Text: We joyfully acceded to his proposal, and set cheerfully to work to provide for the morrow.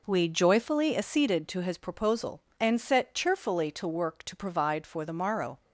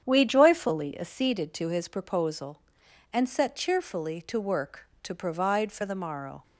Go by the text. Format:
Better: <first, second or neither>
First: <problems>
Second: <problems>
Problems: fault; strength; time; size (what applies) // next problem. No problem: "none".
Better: first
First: none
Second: starts louder than the rest; strong; until 1.0 s; 8.5 dB